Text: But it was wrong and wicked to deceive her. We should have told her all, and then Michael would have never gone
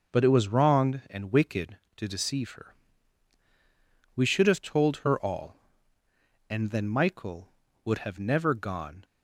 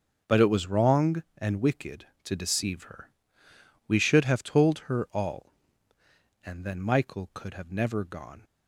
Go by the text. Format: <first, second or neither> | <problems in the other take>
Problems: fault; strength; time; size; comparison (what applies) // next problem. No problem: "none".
first | starts louder than the rest; until 1.4 s; 6.5 dB // says "could" for "would"; at 7.3 s